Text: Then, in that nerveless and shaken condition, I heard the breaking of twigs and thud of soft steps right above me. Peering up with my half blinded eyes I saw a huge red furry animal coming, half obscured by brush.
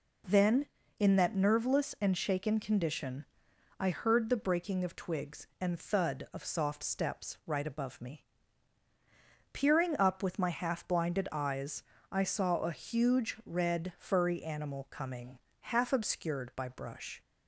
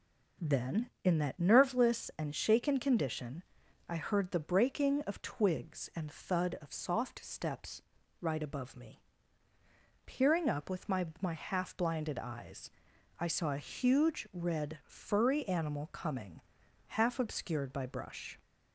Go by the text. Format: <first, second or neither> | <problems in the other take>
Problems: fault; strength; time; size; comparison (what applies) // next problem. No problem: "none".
first | pauses between "steps" and "right"; at 7.8 s; 0.40 s long // says "my" twice; at 11.2 s // pauses between "eyes" and "I"; noticeable; at 12.7 s; 0.48 s long; slight in the first